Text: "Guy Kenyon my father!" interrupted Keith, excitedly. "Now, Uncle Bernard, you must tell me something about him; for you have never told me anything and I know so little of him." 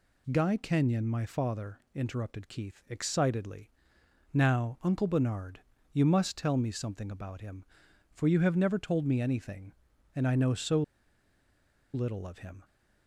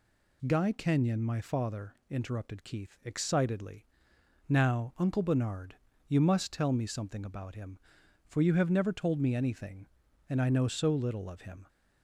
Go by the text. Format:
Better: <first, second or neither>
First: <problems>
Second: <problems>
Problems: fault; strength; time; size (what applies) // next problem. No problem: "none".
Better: second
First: pauses between "so" and "little"; at 10.8 s; 1.1 s long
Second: none